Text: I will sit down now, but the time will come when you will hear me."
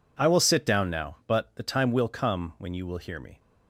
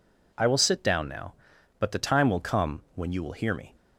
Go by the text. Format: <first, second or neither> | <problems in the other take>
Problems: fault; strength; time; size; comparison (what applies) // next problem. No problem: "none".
neither | none